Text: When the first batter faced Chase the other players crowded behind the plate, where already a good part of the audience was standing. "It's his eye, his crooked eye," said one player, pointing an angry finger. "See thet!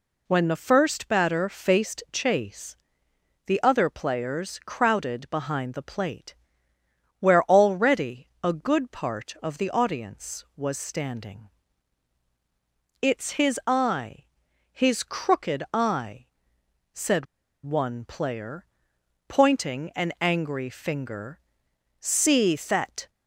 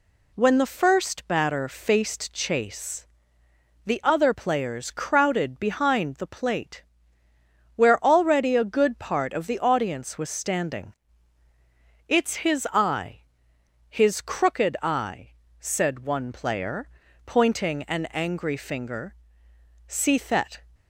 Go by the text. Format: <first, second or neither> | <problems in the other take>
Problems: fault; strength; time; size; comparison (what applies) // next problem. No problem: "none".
second | pauses between "Chase" and "the"; noticeable; at 2.7 s; 0.72 s long; noticeable in the second // pauses between "said" and "one"; at 17.2 s; 0.39 s long